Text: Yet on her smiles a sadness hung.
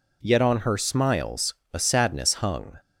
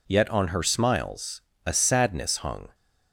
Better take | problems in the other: neither | pauses between "smiles" and "a"; slight; the same in both

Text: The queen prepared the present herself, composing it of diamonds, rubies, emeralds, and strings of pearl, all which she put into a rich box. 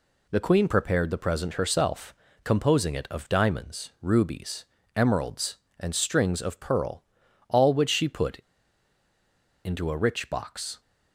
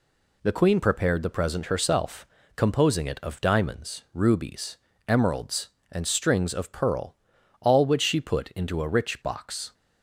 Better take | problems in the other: second | pauses between "put" and "into"; strong; at 8.3 s; 1.2 s long

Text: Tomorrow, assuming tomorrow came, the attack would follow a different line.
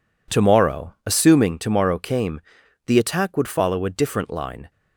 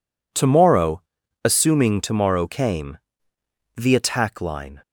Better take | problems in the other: first | skips "would follow a different"; at 4.3 s

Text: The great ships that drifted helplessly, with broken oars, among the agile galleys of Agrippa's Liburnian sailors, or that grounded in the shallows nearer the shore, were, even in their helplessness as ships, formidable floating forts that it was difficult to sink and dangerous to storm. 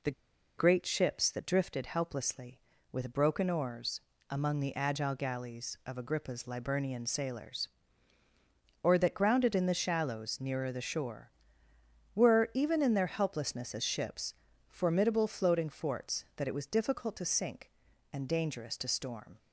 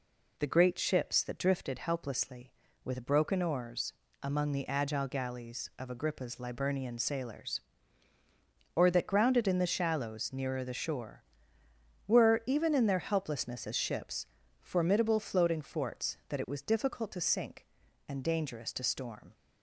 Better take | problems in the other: second | pauses between "The" and "great"; noticeable; at 0.1 s; 0.46 s long

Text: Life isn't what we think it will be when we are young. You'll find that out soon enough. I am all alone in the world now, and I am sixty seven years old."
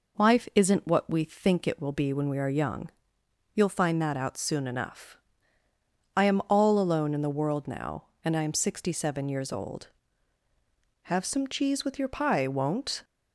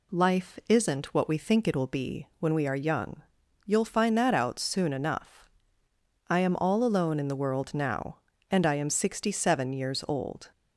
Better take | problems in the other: second | goes on to say "Have some cheese with your pie won't"; strong; from 11.1 s on; 1.9 s long

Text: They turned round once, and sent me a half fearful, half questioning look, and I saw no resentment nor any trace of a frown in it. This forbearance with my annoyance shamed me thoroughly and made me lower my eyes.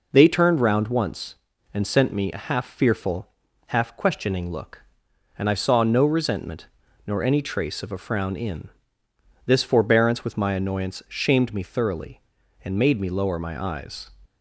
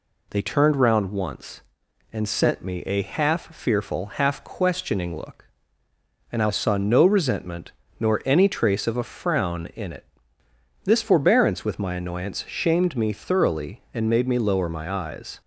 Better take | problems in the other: second | pauses between "resentment" and "nor"; at 6.6 s; 0.38 s long; slight in the second // skips "it"; at 9.0 s

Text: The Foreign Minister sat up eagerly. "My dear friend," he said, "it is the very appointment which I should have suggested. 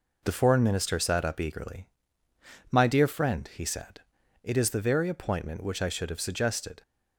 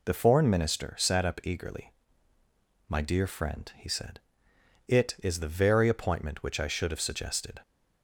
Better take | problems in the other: neither | none

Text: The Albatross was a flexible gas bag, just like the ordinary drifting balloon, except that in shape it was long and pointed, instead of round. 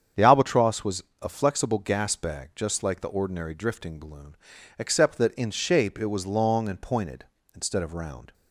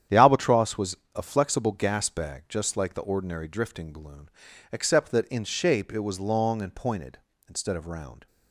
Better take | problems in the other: first | gets quieter; strong; throughout; 10.5 dB // starts louder than the rest; strong; until 1.2 s; 9.5 dB; strong in the first // pauses between "was" and "a"; slight; at 0.9 s; 0.18 s long; slight in the first

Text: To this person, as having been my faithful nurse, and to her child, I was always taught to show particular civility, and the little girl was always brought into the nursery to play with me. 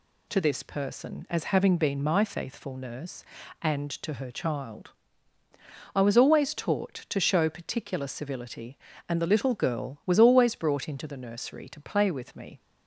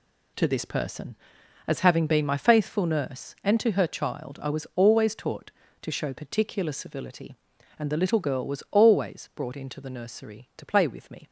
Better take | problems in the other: neither | none

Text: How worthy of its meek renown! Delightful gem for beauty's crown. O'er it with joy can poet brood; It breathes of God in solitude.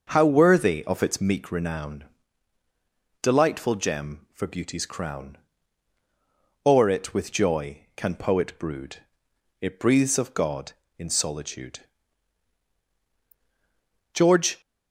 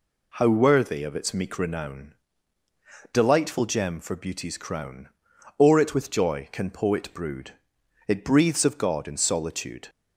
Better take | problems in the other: second | starts louder than the rest; noticeable; until 1.1 s; 6 dB // goes on to say "George"; slight; from 14.1 s on; 0.46 s long

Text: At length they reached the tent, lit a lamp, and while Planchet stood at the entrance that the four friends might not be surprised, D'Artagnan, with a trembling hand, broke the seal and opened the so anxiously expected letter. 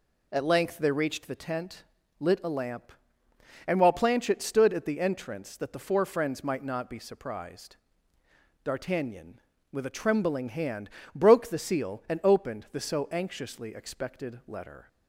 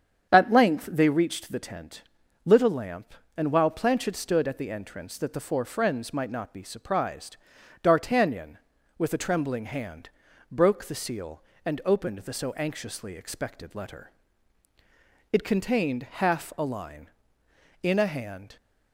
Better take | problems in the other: first | starts louder than the rest; strong; until 1.3 s; 8 dB // goes on to say "It contained half a line in a hand"; strong; from 15.3 s on; 3.2 s long

